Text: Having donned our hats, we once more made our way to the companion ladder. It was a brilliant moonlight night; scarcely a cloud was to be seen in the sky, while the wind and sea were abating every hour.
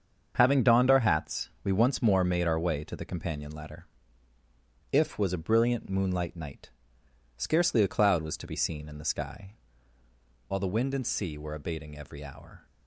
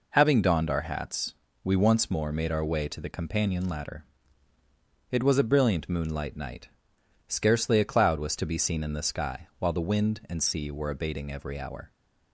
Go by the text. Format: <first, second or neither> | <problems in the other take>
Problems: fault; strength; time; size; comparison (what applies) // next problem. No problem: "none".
second | starts louder than the rest; until 1.3 s; 7 dB // says "If" for "It"; at 4.9 s